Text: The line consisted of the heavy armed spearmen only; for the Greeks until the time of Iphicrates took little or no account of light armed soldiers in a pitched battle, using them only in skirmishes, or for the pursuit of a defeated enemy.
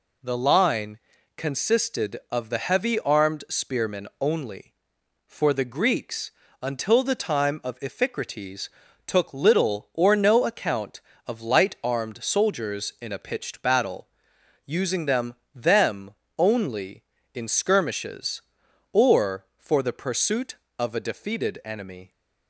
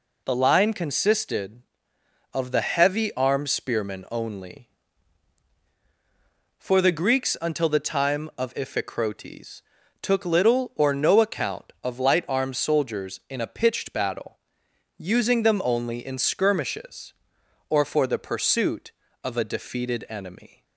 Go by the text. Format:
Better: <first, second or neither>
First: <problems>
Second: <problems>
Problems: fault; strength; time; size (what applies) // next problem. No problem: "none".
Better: second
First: pauses between "line" and "consisted"; at 0.9 s; 0.38 s long // pauses between "Greeks" and "until"; slight; at 6.3 s; 0.28 s long // pauses between "Iphicrates" and "took"; at 8.6 s; 0.38 s long // says "them" twice; at 15.5 s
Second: pauses between "Iphicrates" and "took"; at 9.6 s; 0.40 s long